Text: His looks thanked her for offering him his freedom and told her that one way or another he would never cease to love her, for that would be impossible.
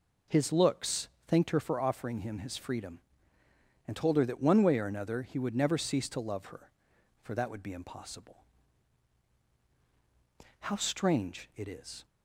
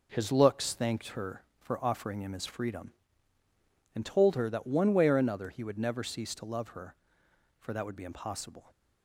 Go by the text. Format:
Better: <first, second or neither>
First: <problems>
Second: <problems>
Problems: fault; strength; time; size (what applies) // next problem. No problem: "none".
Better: second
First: pauses between "looks" and "thanked"; slight; at 1.0 s; 0.18 s long // goes on to say "How strange it is"; from 10.6 s on; 1.4 s long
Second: none